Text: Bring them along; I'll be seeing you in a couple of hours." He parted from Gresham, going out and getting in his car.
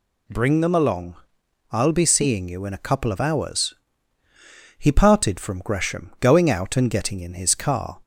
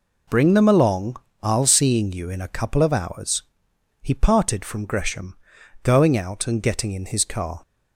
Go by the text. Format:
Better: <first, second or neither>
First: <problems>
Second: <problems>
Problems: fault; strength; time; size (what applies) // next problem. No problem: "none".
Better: first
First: none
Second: skips "be"; at 1.6 s